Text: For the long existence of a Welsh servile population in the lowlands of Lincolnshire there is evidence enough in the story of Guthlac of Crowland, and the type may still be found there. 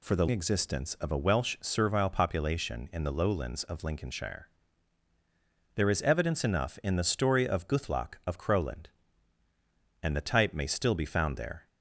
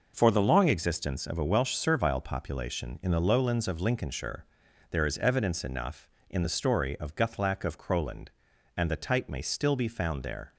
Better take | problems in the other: second | skips "long"; at 0.2 s // pauses between "Lincolnshire" and "there"; strong; at 4.4 s; 1.2 s long; noticeable in the second

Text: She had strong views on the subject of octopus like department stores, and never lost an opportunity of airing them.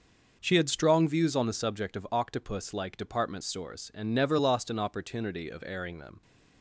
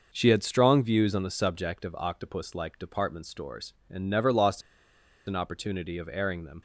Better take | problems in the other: first | pauses between "lost" and "an"; noticeable; at 4.6 s; 0.65 s long

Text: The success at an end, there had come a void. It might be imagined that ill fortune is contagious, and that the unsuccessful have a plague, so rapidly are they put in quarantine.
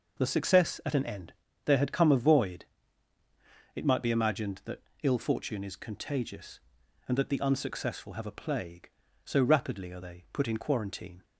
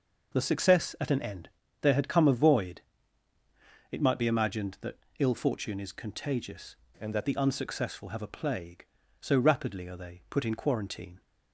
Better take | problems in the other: first | pauses between "that" and "ill"; slight; at 4.9 s; 0.22 s long; slight in the first // changes voice from "and" to "that"; from 7.0 to 7.2 s; 0.2 s long

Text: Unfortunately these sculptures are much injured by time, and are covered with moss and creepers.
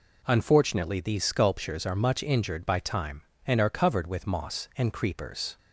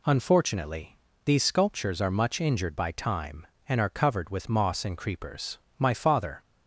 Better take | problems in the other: first | pauses between "Unfortunately" and "these"; slight; at 0.9 s; 0.30 s long // goes on to say "My father"; noticeable; from 5.7 s on; 0.62 s long

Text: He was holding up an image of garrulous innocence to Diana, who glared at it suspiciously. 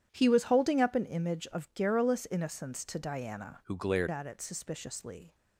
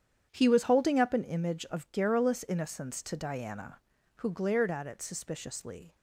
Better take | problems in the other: second | starts louder than the rest; strong; until 1.1 s; 10 dB; strong in the second // changes voice from "who" to "glared"; from 3.6 to 4.0 s; 0.4 s long

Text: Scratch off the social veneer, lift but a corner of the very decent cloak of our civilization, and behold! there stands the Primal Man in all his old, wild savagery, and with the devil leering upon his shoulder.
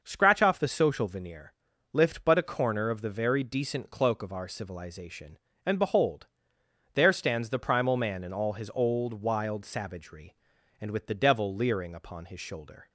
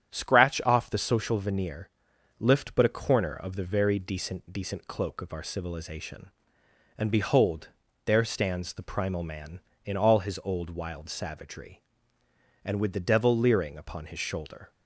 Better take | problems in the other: first | starts louder than the rest; strong; until 1.1 s; 9 dB // says "decent" twice; at 4.5 s

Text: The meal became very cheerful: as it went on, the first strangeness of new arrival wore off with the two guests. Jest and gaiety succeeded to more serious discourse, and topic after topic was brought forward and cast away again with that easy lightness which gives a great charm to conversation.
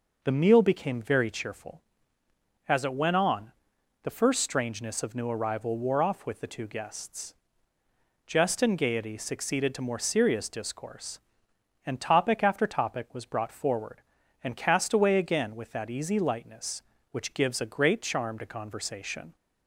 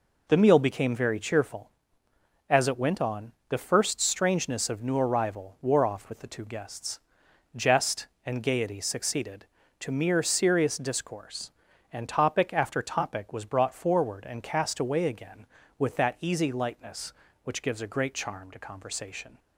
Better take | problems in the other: first | says "mere" for "more"; at 9.9 s

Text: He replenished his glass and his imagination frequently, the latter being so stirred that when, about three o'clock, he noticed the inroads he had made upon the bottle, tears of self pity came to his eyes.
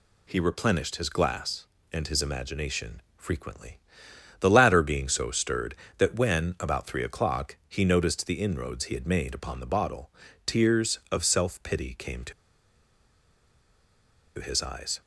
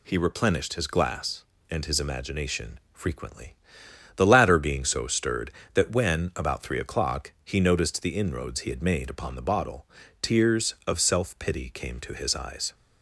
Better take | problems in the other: second | pauses between "imagination" and "frequently"; slight; at 3.0 s; 0.16 s long // pauses between "to" and "his"; strong; at 12.3 s; 2.0 s long

